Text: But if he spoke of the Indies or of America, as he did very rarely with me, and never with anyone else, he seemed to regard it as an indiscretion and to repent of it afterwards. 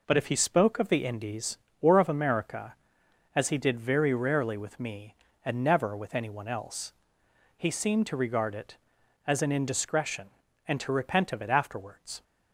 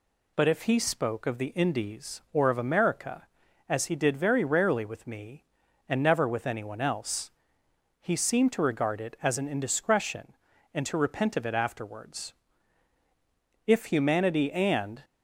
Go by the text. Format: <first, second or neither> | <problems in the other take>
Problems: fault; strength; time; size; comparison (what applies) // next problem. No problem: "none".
first | goes on to say "If humanity and"; from 13.6 s on; 1.3 s long